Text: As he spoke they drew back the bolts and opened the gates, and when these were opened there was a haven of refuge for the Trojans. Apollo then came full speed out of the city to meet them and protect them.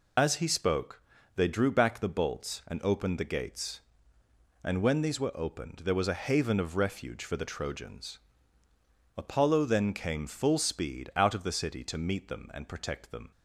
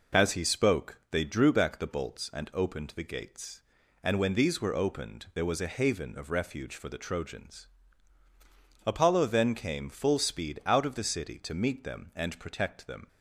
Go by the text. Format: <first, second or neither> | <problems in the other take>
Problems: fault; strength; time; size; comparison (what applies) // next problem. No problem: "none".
second | loses the start of "As"; at 0.1 s; 80 ms // pauses between "spoke" and "they"; slight; at 1.0 s; 0.36 s long